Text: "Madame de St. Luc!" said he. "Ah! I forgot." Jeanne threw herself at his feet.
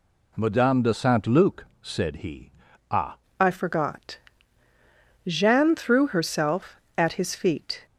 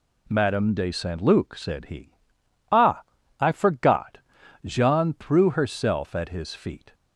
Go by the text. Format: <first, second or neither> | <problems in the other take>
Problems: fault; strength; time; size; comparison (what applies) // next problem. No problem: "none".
second | changes voice at "I"; from 3.4 s on; 4.4 s long